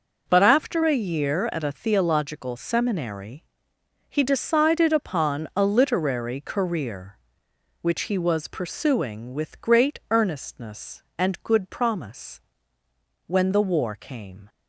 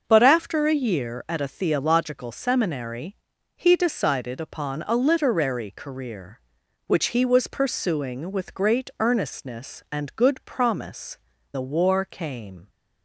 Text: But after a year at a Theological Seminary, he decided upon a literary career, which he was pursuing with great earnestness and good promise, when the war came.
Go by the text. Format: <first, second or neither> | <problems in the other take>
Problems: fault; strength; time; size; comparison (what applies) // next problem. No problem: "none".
first | starts louder than the rest; until 1.0 s; 6.5 dB // skips "when"; at 11.3 s